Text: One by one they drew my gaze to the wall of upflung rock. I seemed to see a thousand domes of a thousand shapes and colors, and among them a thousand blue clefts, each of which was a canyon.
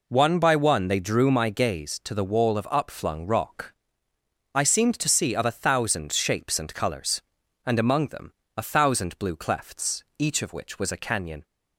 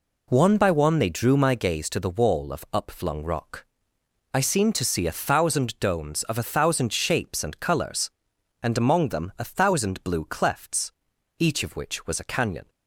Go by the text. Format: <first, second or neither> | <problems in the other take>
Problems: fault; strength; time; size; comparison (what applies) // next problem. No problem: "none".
second | skips "a thousand domes"; at 5.3 s // pauses between "them" and "a"; slight; at 8.3 s; 0.22 s long